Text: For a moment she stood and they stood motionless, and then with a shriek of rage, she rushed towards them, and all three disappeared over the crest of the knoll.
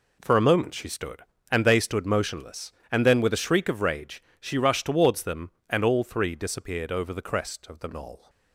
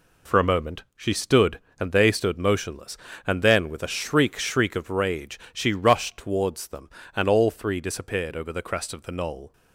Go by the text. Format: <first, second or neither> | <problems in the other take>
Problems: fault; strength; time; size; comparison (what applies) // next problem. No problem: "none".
first | says "shriek" twice; at 4.4 s